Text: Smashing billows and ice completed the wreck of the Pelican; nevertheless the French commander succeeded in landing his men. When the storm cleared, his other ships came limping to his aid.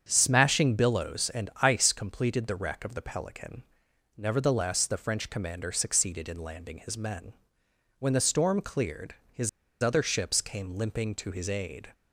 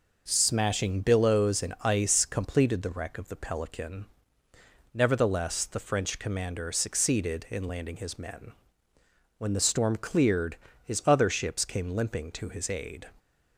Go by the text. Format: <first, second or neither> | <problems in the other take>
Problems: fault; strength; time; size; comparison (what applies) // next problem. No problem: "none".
second | starts louder than the rest; strong; until 1.0 s; 7.5 dB // pauses between "his" and "other"; slight; at 9.4 s; 0.32 s long